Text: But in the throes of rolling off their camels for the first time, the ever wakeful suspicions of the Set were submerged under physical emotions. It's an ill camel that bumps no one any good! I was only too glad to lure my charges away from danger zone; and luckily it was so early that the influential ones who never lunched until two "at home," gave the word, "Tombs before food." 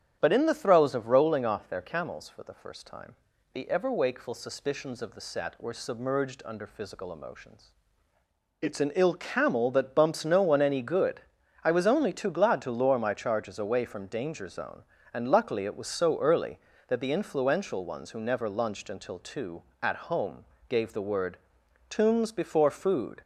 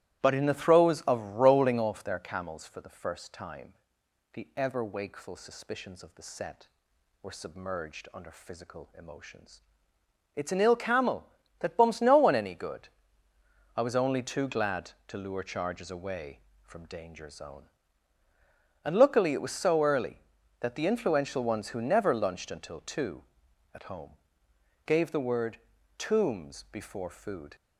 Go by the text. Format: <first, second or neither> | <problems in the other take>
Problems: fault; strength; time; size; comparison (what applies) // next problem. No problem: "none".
first | starts louder than the rest; strong; until 1.2 s; 15.5 dB; strong in the first // skips "my"; at 15.4 s